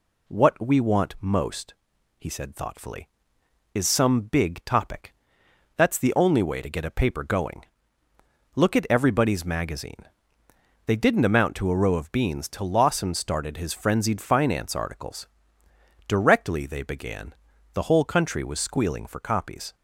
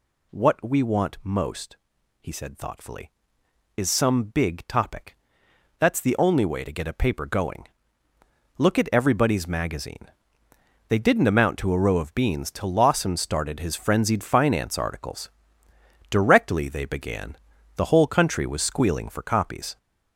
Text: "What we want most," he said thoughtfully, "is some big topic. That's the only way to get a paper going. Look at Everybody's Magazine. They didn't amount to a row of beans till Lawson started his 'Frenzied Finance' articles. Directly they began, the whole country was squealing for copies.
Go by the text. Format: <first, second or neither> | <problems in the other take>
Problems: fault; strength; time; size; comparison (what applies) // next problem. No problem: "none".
first | gets louder; noticeable; throughout; 6 dB